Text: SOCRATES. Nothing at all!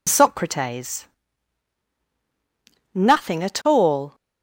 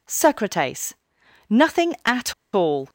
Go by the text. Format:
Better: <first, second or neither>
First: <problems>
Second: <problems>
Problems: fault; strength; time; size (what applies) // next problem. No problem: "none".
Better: first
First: none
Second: pauses between "at" and "all"; slight; at 2.3 s; 0.21 s long